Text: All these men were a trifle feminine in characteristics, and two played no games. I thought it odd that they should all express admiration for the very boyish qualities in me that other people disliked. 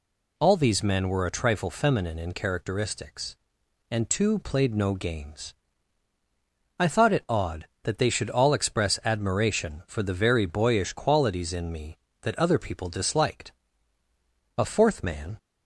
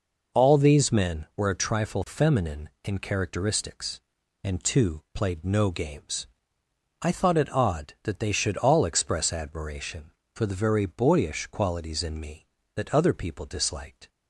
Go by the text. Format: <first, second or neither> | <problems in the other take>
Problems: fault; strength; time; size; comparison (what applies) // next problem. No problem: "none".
second | goes on to say "A fourth man"; noticeable; from 14.5 s on; 0.80 s long